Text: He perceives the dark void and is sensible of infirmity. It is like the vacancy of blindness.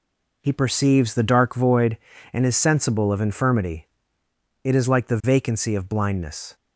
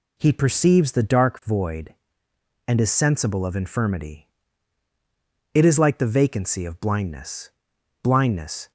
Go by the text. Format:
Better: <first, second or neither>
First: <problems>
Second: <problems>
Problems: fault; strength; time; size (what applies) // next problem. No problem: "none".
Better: first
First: none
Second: says "blindness" twice; at 8.0 s